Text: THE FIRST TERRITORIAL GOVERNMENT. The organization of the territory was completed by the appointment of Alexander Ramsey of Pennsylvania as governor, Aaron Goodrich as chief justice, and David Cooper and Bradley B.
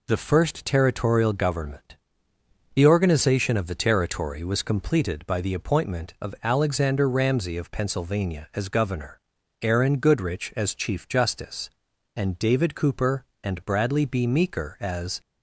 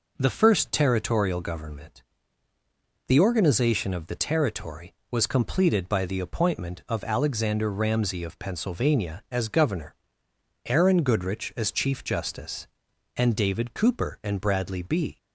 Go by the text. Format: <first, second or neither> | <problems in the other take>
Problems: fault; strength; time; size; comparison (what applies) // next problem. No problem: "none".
second | goes on to say "Meeker as"; noticeable; from 14.2 s on; 0.94 s long